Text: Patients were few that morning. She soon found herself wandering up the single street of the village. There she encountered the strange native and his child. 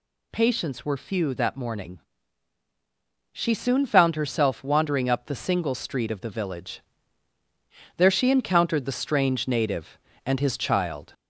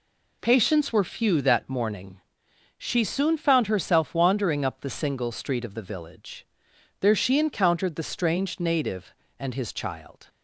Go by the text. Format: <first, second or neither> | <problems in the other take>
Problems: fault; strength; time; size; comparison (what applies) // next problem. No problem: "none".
second | gets louder; slight; throughout; 2 dB